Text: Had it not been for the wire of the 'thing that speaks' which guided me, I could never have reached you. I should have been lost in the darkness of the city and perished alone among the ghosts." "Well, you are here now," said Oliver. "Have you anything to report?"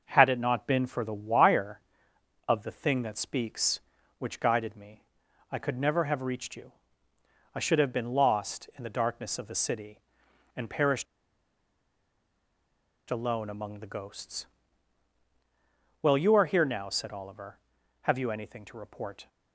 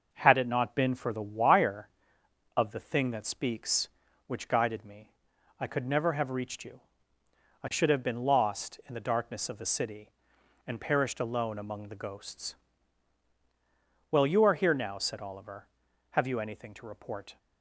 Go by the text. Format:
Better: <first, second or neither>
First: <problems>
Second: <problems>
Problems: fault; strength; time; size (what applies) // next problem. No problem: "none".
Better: second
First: pauses between "perished" and "alone"; strong; at 11.0 s; 2.0 s long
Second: none